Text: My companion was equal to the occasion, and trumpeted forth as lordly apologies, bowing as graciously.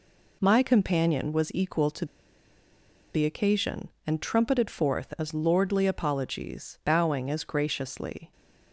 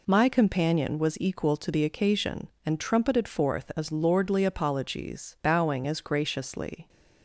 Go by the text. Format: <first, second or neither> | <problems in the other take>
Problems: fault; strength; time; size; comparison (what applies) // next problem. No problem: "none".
second | pauses between "to" and "the"; at 2.0 s; 1.0 s long